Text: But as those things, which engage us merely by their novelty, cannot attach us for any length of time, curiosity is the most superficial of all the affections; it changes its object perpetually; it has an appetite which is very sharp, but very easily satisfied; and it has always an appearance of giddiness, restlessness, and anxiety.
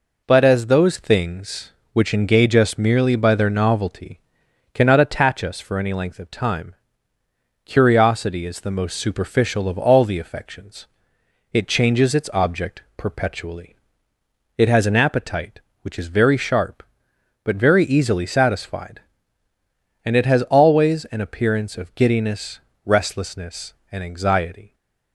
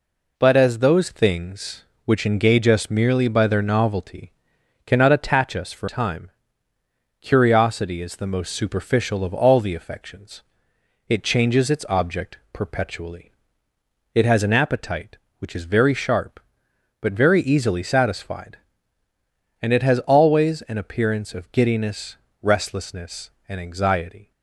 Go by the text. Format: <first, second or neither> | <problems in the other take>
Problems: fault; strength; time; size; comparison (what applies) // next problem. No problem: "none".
first | skips "any length of"; at 5.8 s